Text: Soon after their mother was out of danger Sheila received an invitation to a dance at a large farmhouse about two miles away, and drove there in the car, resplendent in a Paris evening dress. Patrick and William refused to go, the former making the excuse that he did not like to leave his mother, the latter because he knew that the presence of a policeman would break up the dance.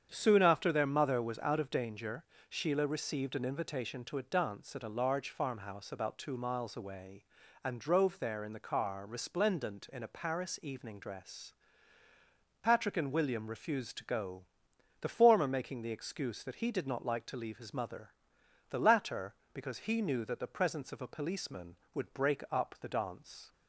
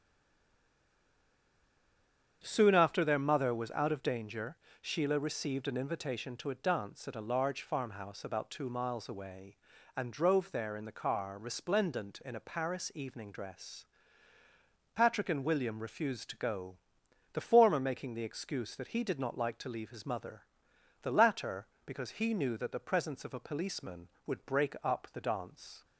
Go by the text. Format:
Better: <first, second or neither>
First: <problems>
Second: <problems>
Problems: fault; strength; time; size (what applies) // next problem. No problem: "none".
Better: first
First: starts louder than the rest; strong; until 1.1 s; 8 dB // pauses between "danger" and "Sheila"; slight; at 2.2 s; 0.24 s long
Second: stays silent before the first word; until 2.4 s; 2.4 s long // starts louder than the rest; strong; until 3.4 s; 8 dB // pauses between "danger" and "Sheila"; slight; at 4.5 s; 0.24 s long